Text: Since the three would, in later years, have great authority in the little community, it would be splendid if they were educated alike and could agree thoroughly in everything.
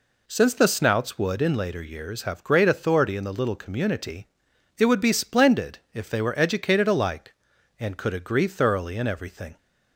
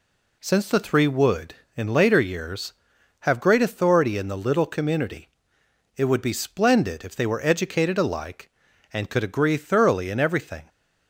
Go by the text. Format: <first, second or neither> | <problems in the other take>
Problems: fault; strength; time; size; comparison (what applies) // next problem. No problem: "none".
second | says "snouts" for "three"; at 0.6 s // pauses between "splendid" and "if"; slight; at 5.7 s; 0.16 s long